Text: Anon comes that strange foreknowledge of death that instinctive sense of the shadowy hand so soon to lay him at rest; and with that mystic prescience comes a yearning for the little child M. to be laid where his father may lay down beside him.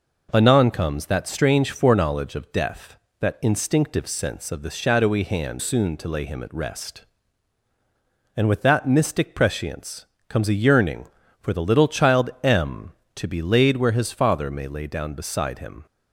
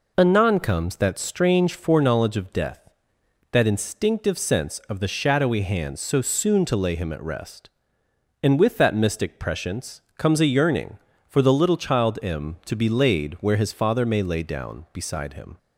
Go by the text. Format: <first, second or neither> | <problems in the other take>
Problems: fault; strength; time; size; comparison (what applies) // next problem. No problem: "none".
second | skips "so"; at 5.5 s // pauses between "prescience" and "comes"; slight; at 10.0 s; 0.24 s long